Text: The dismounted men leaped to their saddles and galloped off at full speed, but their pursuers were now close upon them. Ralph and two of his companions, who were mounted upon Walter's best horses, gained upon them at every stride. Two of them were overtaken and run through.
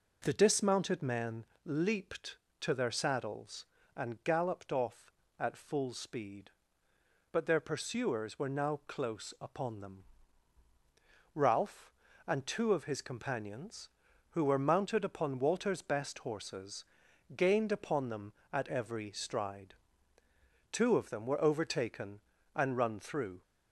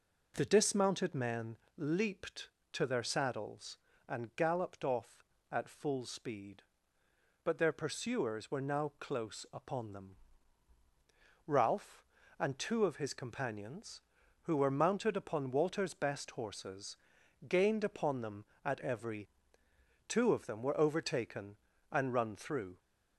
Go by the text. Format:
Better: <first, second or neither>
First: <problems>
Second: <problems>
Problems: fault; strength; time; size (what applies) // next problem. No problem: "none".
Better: first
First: pauses between "men" and "leaped"; slight; at 1.4 s; 0.22 s long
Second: pauses between "men" and "leaped"; slight; at 1.5 s; 0.22 s long // skips "stride"; at 19.6 s